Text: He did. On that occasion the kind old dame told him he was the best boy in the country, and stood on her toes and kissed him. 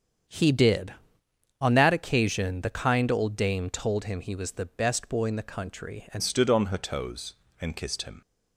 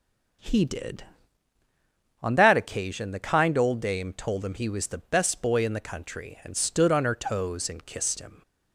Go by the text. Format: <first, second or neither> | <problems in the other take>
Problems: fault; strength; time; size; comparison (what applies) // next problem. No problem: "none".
second | starts louder than the rest; strong; until 1.9 s; 8 dB; also in the second // changes voice at "stood"; from 6.2 s on; 2.0 s long